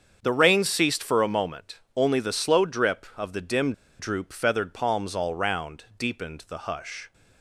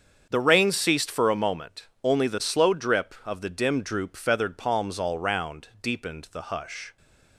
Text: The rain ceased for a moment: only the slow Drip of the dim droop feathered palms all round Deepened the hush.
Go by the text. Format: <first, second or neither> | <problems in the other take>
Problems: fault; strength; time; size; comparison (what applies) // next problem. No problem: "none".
second | starts louder than the rest; strong; until 1.2 s; 7 dB; strong in the second // pauses between "dim" and "droop"; slight; at 3.7 s; 0.27 s long